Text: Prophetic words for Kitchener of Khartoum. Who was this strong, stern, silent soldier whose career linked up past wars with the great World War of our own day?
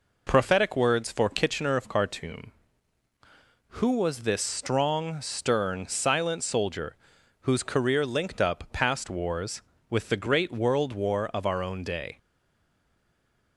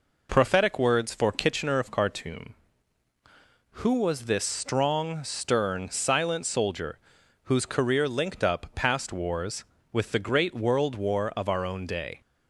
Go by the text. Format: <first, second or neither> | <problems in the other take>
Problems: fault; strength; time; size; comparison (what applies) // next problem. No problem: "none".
second | pauses between "soldier" and "whose"; noticeable; at 6.9 s; 0.48 s long; noticeable in the second // stays silent after the last word; noticeable; from 12.1 s on; 1.4 s long